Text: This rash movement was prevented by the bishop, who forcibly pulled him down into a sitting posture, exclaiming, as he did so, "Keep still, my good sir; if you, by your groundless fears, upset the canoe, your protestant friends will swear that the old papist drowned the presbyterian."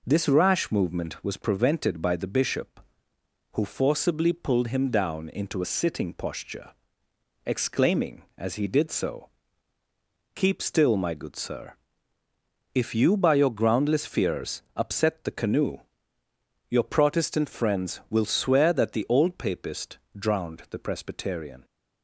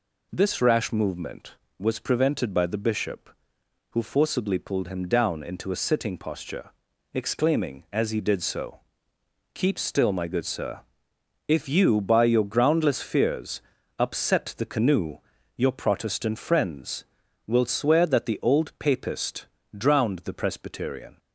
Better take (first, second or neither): neither